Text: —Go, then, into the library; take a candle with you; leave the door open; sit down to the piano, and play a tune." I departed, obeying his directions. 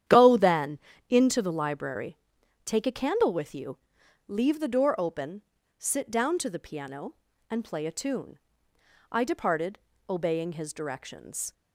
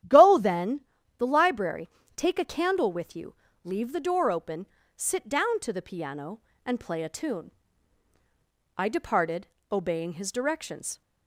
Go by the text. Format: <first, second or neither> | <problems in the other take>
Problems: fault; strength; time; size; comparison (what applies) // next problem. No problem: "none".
first | starts louder than the rest; strong; until 1.4 s; 11 dB; strong in the first // skips "into"; at 0.9 s